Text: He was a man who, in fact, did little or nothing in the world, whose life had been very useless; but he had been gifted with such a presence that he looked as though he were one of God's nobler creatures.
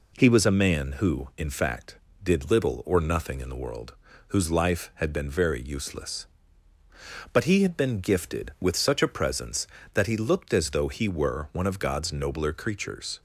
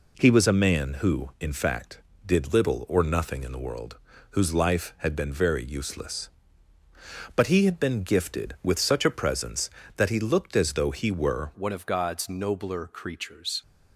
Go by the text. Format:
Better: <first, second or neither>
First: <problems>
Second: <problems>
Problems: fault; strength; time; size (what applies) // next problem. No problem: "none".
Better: first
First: none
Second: changes voice at "one"; from 11.5 s on; 2.1 s long